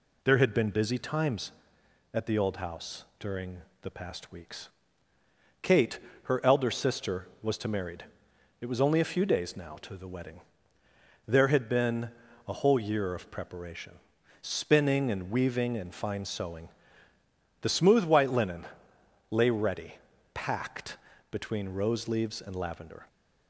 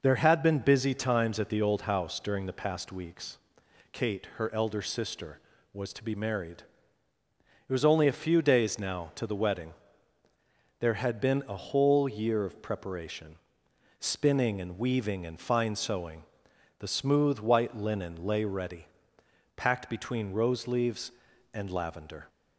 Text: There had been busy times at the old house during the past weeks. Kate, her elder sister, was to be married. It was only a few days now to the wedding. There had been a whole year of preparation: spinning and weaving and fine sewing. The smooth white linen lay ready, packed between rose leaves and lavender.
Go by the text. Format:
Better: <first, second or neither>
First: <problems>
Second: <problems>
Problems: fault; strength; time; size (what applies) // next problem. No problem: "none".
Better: second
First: pauses between "during" and "the"; slight; at 3.6 s; 0.20 s long // skips "be"; at 7.6 s // pauses between "been" and "a"; at 12.0 s; 0.38 s long // pauses between "linen" and "lay"; noticeable; at 18.6 s; 0.66 s long // pauses between "packed" and "between"; slight; at 20.9 s; 0.34 s long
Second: none